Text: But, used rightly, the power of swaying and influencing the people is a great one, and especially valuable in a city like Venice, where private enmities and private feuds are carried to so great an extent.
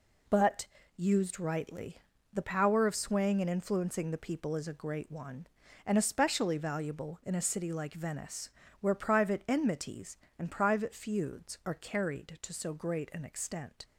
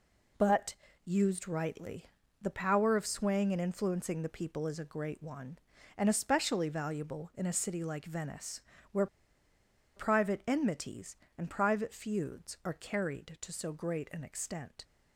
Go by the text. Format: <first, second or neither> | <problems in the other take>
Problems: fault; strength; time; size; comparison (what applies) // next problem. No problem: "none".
first | pauses between "where" and "private"; noticeable; at 9.0 s; 0.90 s long